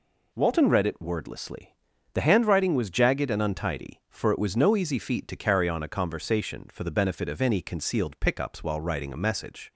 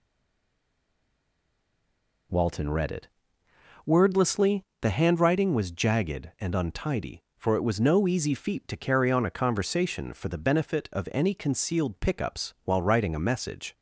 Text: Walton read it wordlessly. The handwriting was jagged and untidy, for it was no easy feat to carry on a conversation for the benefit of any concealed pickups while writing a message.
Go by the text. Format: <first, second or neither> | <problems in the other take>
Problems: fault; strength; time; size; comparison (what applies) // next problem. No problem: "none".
first | stays silent before the first word; until 2.2 s; 2.2 s long // pauses between "it" and "wordlessly"; noticeable; at 3.0 s; 0.76 s long